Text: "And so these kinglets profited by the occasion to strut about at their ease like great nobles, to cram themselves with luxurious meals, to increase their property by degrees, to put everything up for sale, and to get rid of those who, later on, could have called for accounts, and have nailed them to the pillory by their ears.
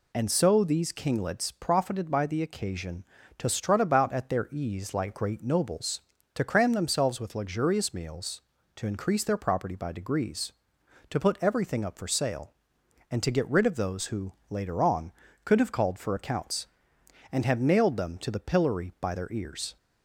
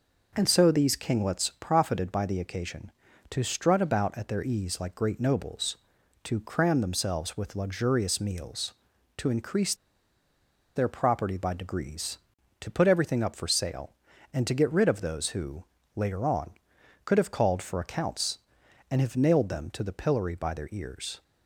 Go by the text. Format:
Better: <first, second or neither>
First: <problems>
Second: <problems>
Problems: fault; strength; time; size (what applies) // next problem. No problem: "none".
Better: first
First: none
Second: pauses between "increase" and "their"; at 9.7 s; 1.0 s long